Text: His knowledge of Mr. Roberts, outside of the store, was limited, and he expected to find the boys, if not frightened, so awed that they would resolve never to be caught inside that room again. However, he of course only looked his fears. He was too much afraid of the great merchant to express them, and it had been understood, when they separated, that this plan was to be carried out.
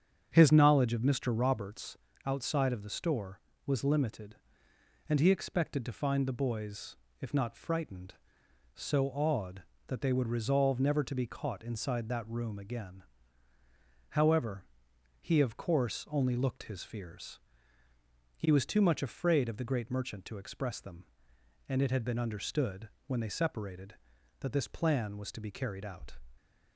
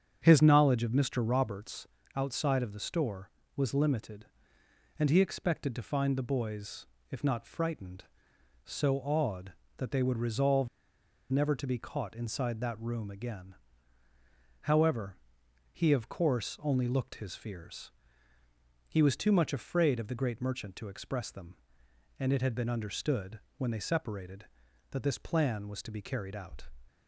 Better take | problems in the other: first | starts louder than the rest; strong; until 1.2 s; 7.5 dB; strong in the first // pauses between "resolve" and "never"; noticeable; at 10.6 s; 0.64 s long

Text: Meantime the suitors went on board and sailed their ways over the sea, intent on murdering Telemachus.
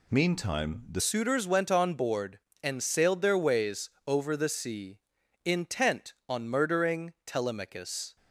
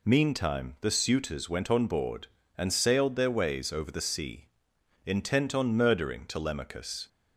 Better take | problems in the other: second | changes voice at "suitors"; from 0.9 s on; 7.2 s long // pauses between "ways" and "over"; slight; at 3.8 s; 0.16 s long

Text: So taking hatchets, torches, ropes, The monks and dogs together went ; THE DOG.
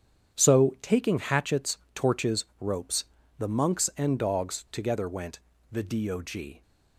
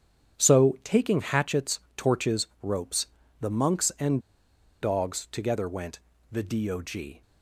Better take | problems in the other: first | starts louder than the rest; strong; until 1.4 s; 8.5 dB; strong in the first // pauses between "and" and "dogs"; noticeable; at 4.2 s; 0.61 s long

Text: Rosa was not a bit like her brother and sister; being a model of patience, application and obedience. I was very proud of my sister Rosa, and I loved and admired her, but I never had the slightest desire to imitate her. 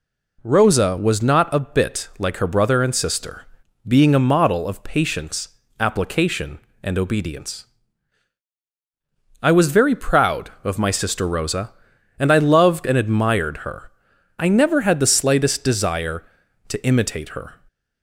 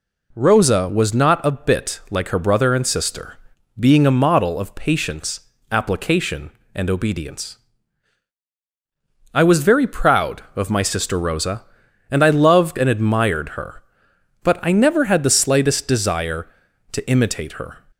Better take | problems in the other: second | skips "but"; at 14.1 s

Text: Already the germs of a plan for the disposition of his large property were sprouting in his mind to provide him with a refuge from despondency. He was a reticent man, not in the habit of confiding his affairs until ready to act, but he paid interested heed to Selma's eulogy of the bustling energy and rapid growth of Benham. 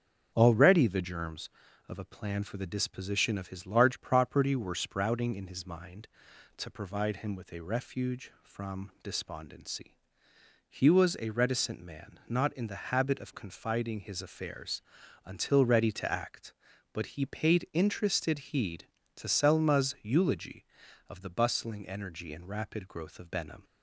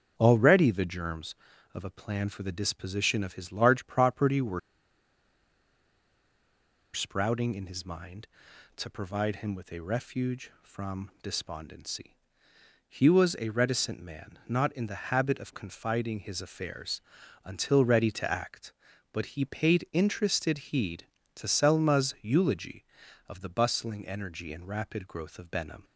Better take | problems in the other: first | starts louder than the rest; until 1.1 s; 6.5 dB; also in the first // pauses between "were" and "sprouting"; strong; at 4.5 s; 2.3 s long // pauses between "affairs" and "until"; at 17.0 s; 0.44 s long; also in the first

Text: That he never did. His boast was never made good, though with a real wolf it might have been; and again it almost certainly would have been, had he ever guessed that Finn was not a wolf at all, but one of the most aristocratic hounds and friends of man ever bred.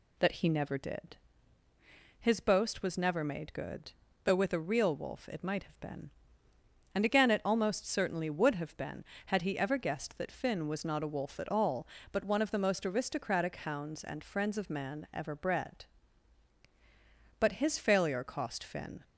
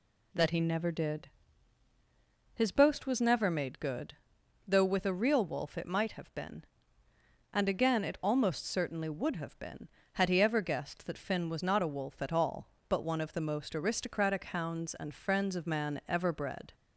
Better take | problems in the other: second | goes on to say "But his failure cost Finn"; from 17.4 s on; 1.6 s long

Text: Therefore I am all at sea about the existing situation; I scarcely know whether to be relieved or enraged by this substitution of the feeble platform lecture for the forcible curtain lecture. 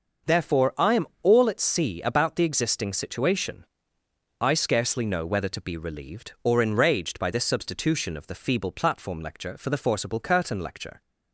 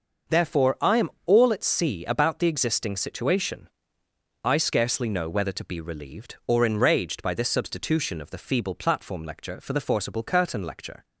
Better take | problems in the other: neither | starts louder than the rest; noticeable; the same in both // pauses between "am" and "all"; slight; the same in both

